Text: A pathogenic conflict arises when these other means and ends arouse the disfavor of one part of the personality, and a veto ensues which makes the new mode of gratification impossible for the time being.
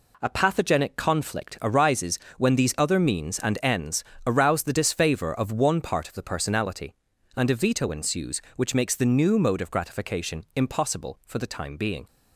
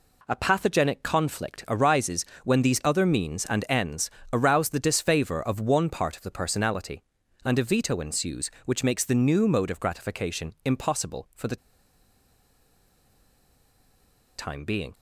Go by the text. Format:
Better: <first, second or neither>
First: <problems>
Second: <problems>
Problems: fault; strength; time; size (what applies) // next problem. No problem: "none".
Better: first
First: pauses between "arises" and "when"; slight; at 2.1 s; 0.20 s long // pauses between "ends" and "arouse"; slight; at 4.0 s; 0.22 s long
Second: pauses between "arises" and "when"; slight; at 2.2 s; 0.20 s long // pauses between "ends" and "arouse"; slight; at 4.0 s; 0.22 s long // pauses between "the" and "time"; strong; at 11.5 s; 2.8 s long